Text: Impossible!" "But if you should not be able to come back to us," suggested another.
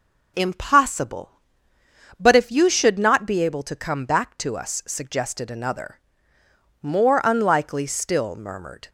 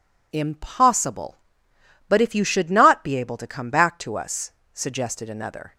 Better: second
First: goes on to say "More unlikely still murmured"; strong; from 6.8 s on; 2.0 s long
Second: none

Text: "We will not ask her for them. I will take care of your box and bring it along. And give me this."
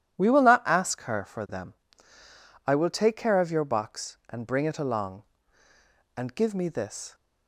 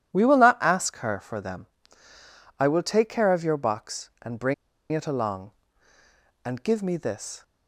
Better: first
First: none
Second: pauses between "bring" and "it"; at 4.5 s; 0.38 s long

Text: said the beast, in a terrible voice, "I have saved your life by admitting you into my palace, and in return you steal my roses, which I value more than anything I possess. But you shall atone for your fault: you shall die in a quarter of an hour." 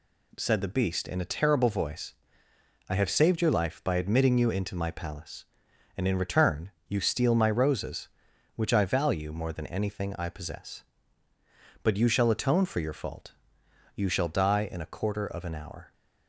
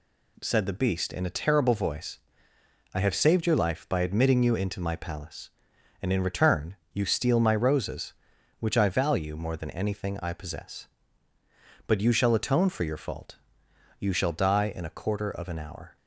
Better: neither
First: pauses between "return" and "you"; slight; at 6.6 s; 0.18 s long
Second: pauses between "return" and "you"; slight; at 6.7 s; 0.18 s long

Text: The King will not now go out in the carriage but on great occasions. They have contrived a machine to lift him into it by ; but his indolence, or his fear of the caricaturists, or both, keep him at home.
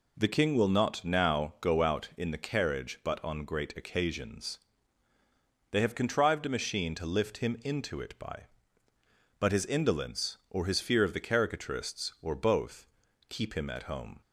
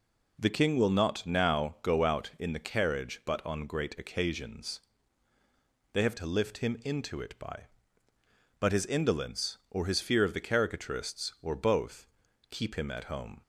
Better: first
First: none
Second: skips "contrived a machine"; at 6.1 s

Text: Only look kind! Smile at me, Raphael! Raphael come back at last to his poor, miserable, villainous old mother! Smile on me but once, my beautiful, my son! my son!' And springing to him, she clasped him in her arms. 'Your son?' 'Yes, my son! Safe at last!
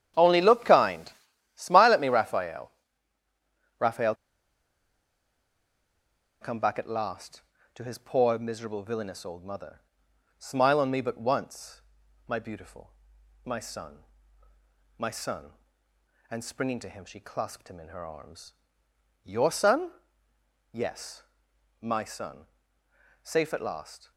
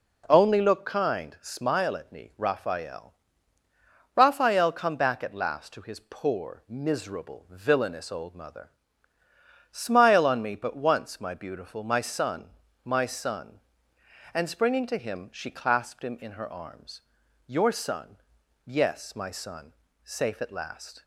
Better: second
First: starts louder than the rest; strong; until 1.6 s; 10 dB // pauses between "Raphael" and "come"; strong; at 4.1 s; 2.2 s long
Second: none

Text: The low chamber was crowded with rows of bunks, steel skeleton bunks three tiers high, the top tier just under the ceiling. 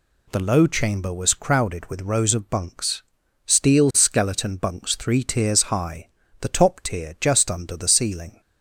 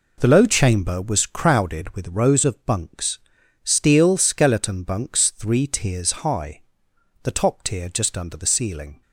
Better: neither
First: none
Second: none

